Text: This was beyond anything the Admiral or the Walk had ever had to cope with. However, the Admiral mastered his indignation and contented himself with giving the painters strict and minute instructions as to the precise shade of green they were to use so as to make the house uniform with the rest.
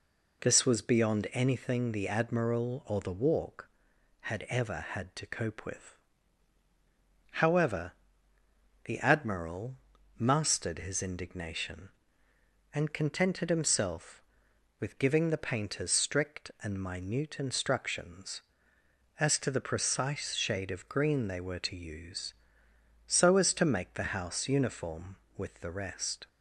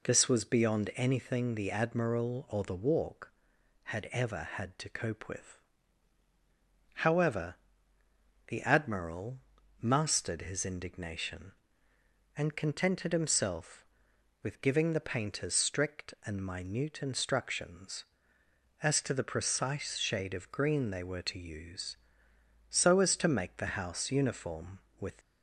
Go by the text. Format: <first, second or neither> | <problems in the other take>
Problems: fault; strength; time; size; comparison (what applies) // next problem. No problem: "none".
first | pauses between "Admiral" and "mastered"; at 9.3 s; 0.42 s long; also in the first // stops before "the rest"; at 25.2 s